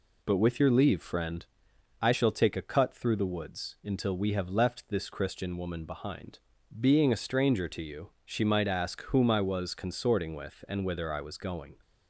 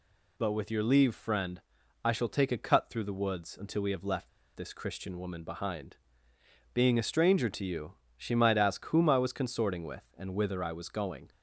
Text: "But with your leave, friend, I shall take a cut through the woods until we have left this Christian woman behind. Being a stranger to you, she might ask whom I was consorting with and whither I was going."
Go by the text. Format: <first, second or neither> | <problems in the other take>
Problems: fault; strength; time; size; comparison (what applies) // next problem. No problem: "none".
first | pauses between "left" and "this"; slight; at 4.2 s; 0.27 s long